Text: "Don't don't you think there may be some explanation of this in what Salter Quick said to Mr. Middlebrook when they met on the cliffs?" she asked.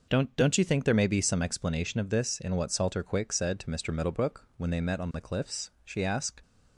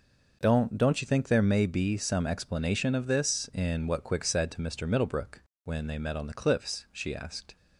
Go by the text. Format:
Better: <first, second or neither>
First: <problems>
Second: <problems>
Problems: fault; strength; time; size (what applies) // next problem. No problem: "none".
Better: first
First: none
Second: skips "Salter"; at 4.0 s // pauses between "Middlebrook" and "when"; slight; at 5.4 s; 0.22 s long